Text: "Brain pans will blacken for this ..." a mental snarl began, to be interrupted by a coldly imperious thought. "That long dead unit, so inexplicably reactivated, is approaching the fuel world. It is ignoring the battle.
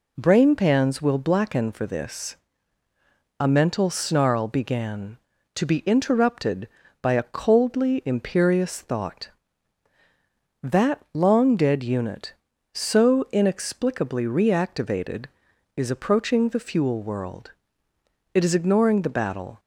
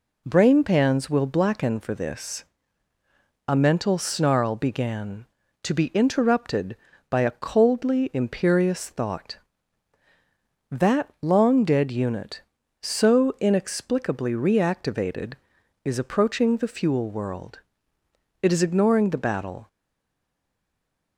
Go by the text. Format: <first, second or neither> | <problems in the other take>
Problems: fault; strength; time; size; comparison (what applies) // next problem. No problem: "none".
first | stays silent after the last word; noticeable; from 19.6 s on; 1.5 s long